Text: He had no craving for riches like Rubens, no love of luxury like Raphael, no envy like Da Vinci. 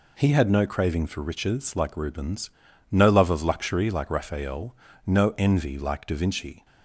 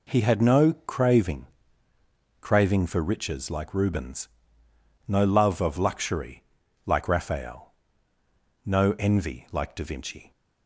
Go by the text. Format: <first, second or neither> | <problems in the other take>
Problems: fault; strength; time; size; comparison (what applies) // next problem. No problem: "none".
first | says "craving" twice; at 2.4 s // pauses between "luxury" and "like"; at 6.4 s; 0.40 s long